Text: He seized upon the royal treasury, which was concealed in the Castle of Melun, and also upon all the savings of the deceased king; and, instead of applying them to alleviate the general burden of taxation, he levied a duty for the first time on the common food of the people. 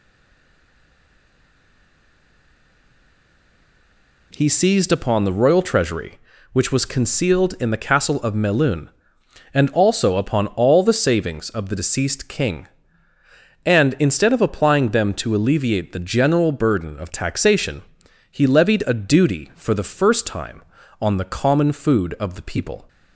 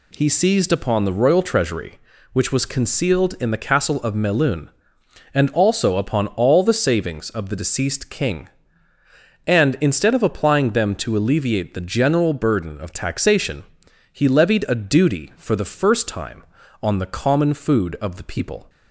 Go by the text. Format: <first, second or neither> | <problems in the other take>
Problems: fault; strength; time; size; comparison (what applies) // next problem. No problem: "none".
second | stays silent before the first word; strong; until 4.3 s; 4.3 s long